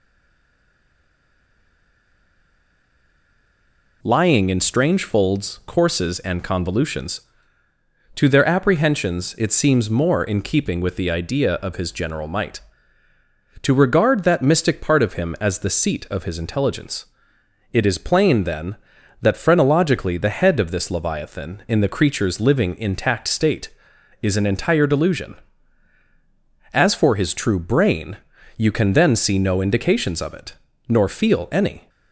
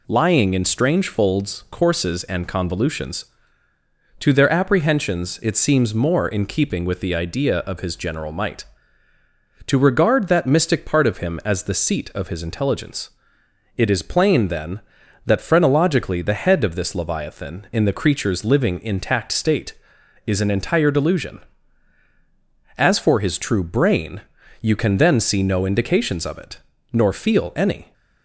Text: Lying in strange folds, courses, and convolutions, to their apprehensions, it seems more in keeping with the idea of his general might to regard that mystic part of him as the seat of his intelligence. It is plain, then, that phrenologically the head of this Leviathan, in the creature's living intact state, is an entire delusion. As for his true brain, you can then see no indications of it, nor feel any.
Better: second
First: stays silent before the first word; strong; until 4.0 s; 4.0 s long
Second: none

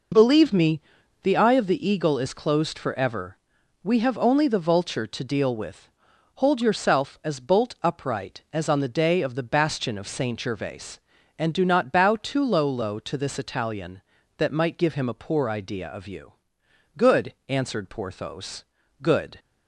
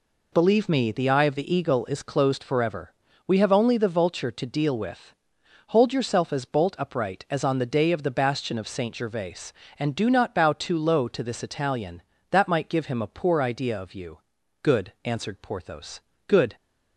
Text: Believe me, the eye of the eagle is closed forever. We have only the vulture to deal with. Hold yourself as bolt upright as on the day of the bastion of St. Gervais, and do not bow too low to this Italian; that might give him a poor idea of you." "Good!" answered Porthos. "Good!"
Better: second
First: says "low" twice; at 12.6 s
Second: none

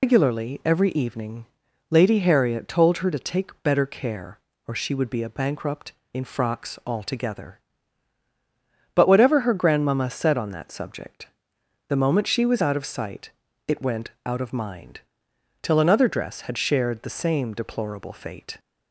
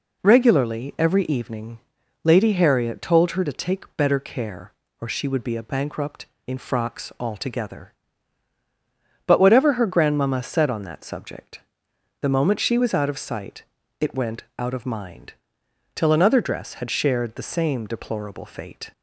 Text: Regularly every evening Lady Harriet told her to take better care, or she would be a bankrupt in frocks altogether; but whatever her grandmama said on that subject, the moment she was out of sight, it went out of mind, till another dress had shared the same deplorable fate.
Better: second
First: loses the start of "Regularly"; at 0.0 s; 145 ms // pauses between "evening" and "Lady"; at 1.4 s; 0.44 s long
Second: pauses between "evening" and "Lady"; at 1.7 s; 0.44 s long

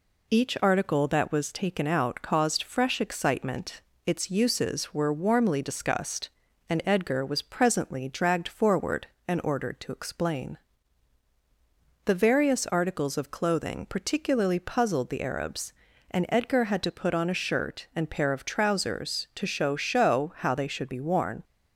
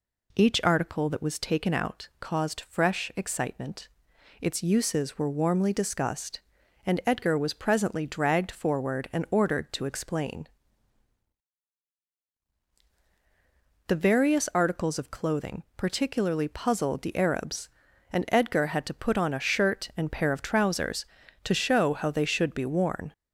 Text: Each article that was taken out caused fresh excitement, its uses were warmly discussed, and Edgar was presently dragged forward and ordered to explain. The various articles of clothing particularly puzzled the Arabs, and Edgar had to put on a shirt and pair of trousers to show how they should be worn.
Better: second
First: says "show" twice; at 19.7 s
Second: none

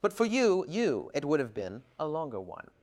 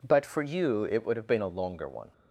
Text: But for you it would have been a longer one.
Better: second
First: says "you" twice; at 0.6 s // pauses between "been" and "a"; slight; at 1.8 s; 0.16 s long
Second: none

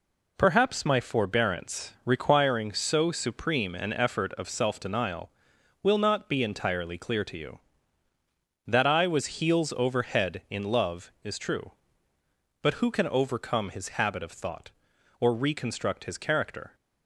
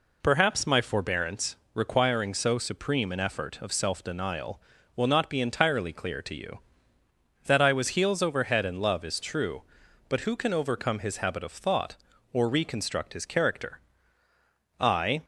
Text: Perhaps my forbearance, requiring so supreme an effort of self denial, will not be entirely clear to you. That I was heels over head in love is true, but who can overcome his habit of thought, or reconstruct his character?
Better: first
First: none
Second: goes on to say "I"; slight; from 14.8 s on; 0.42 s long

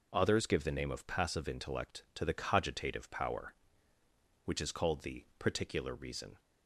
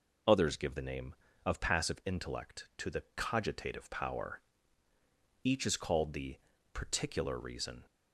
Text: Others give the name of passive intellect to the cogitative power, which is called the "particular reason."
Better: first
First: none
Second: says "each" for "which"; at 5.4 s // pauses between "the" and "particular"; slight; at 6.3 s; 0.36 s long

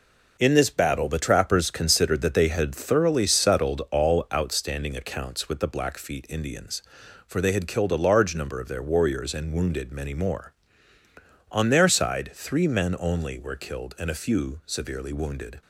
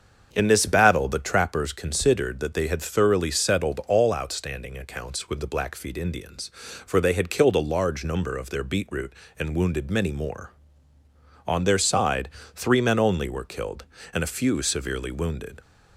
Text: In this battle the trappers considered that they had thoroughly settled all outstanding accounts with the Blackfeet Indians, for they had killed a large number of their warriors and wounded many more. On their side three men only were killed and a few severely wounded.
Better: first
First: none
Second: starts louder than the rest; until 1.3 s; 7 dB // says "beetroot" for "warriors"; at 8.6 s // pauses between "side" and "three"; slight; at 12.2 s; 0.26 s long

